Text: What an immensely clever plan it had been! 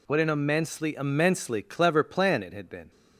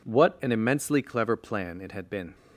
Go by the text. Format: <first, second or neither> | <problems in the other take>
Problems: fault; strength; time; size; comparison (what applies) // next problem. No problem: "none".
second | says "immensely" twice; at 0.9 s